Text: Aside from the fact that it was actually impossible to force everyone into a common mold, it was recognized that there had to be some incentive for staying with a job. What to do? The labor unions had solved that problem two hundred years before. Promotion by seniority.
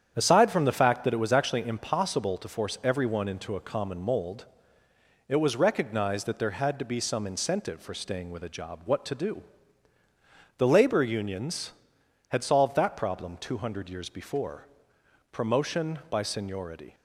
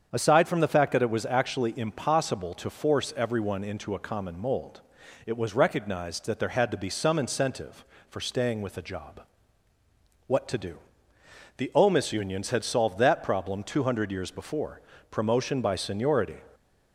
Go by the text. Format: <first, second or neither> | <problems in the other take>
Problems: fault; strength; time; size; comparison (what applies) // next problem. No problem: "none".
first | starts louder than the rest; strong; until 1.1 s; 7.5 dB; strong in the first // says "omis" for "labor"; at 11.7 s